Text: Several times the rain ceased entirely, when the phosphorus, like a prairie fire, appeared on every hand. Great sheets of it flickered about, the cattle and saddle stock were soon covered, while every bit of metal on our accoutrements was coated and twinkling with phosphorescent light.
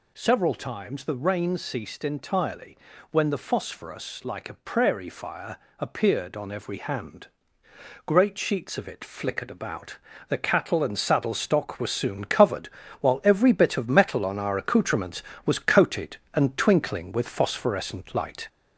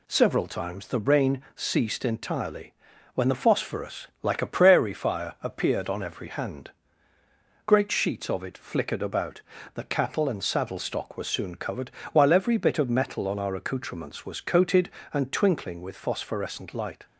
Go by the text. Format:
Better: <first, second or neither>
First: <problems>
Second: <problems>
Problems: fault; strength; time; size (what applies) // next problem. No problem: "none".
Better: second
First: gets louder; throughout; 3.5 dB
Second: none